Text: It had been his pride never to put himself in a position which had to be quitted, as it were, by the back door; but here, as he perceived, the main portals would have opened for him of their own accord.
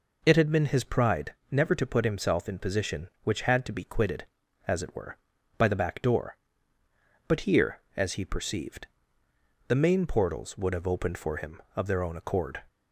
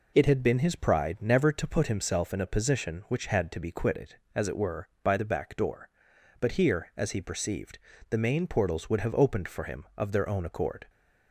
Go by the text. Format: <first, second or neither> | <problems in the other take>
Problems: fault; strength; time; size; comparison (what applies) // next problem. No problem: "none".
second | pauses between "pride" and "never"; slight; at 1.3 s; 0.16 s long // skips "a"; at 2.5 s